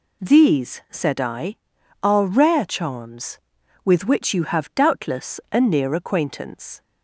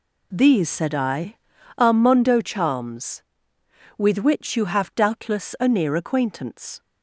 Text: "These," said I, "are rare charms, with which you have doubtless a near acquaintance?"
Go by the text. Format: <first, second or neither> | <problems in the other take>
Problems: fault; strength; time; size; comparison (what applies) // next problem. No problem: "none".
first | says "mondo" for "rare"; at 1.9 s